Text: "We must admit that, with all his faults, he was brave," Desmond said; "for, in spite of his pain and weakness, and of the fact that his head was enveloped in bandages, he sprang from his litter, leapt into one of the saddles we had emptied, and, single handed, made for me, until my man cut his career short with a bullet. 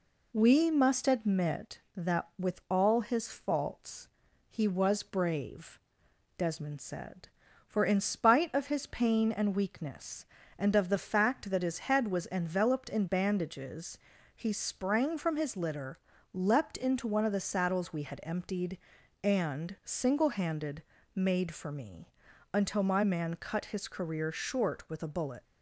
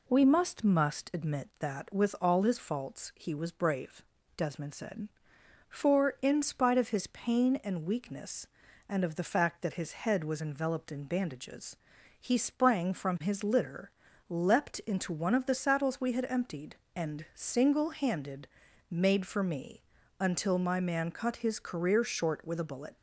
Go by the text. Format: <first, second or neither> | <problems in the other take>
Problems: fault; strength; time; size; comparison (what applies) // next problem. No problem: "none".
first | says "must" twice; at 0.6 s